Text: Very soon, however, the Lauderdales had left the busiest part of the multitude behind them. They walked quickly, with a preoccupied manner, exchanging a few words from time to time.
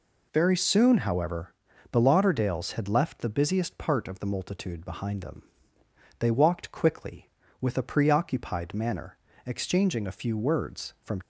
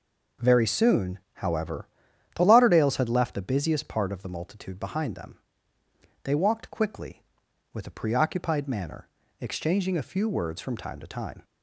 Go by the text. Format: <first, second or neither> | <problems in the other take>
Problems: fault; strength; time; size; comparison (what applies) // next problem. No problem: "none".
second | stops before "time to time"; at 11.2 s